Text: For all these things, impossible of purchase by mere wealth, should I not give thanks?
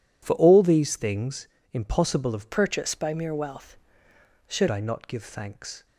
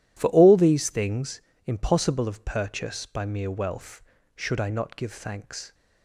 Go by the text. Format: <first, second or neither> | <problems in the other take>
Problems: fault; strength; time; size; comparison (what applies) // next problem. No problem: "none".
second | changes voice from "purchase" to "should"; from 2.5 to 4.6 s; 2.1 s long